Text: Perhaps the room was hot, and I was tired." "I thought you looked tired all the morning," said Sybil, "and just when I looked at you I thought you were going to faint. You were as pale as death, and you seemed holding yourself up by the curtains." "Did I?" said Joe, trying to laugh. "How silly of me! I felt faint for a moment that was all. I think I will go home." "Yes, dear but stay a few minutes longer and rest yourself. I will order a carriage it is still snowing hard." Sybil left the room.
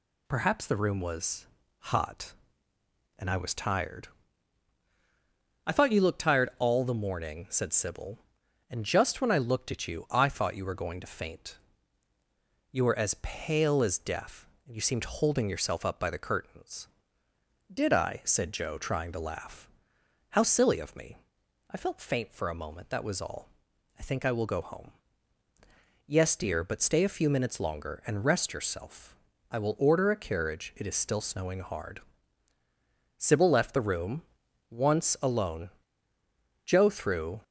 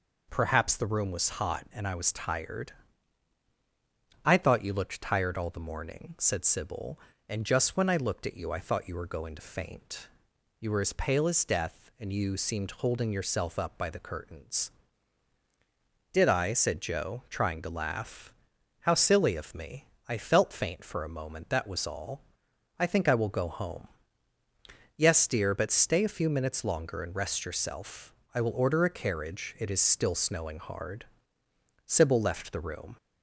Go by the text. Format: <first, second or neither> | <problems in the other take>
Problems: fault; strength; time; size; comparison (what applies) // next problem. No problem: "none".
second | pauses between "was" and "hot"; slight; at 1.4 s; 0.34 s long // goes on to say "Once alone Joe threw"; strong; from 34.6 s on; 2.7 s long